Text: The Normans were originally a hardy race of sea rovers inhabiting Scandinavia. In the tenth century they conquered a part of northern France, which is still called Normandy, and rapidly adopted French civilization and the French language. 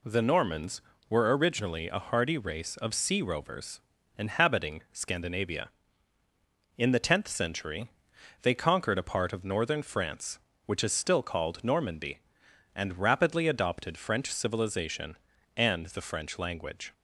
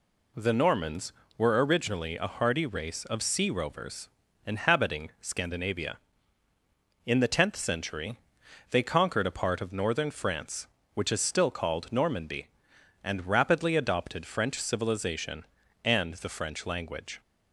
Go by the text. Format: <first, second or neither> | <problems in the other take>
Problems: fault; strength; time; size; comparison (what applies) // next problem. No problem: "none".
neither | pauses between "rovers" and "inhabiting"; slight; the same in both // pauses between "century" and "they"; noticeable; the same in both